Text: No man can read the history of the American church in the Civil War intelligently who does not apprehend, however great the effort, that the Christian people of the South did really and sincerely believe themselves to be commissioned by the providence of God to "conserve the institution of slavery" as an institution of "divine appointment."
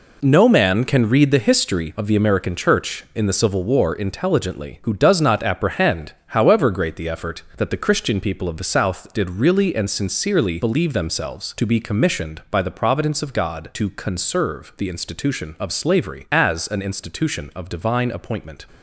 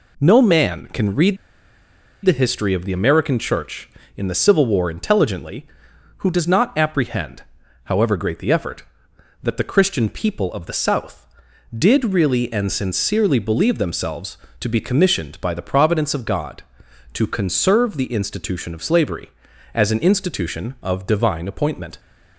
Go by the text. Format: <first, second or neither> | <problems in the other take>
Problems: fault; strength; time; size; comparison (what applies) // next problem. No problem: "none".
first | pauses between "read" and "the"; noticeable; at 1.3 s; 0.88 s long